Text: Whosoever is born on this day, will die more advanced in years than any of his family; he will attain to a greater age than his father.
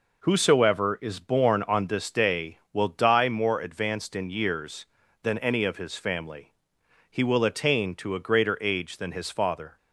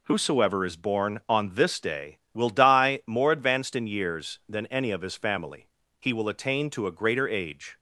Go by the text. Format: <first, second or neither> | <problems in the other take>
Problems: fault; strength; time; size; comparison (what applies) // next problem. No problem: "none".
first | stops before "than his father"; at 7.7 s